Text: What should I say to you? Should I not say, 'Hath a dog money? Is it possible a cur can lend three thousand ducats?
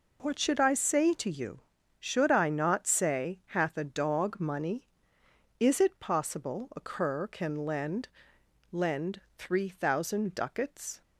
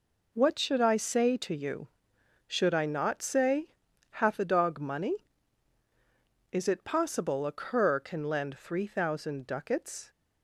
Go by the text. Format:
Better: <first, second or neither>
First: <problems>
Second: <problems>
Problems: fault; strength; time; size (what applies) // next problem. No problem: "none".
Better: second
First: says "lend" twice; at 8.7 s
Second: none